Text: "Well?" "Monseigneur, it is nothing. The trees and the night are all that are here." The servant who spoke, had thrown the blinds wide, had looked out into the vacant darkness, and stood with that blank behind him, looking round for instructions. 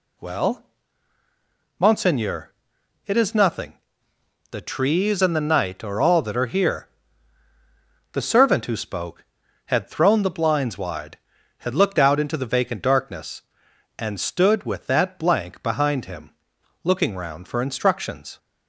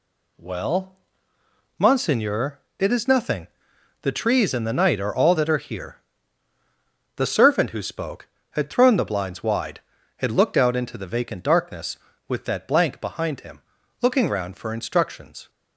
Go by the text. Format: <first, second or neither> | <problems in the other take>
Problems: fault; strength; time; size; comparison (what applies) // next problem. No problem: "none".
first | skips "and stood"; at 12.1 s